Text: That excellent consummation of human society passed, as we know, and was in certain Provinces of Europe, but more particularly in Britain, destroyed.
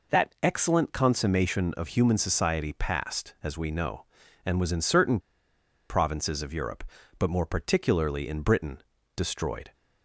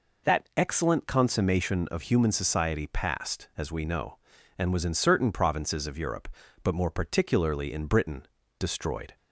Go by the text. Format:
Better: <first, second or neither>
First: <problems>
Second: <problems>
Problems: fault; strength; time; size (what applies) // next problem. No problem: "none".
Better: second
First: pauses between "certain" and "Provinces"; noticeable; at 5.1 s; 0.70 s long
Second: none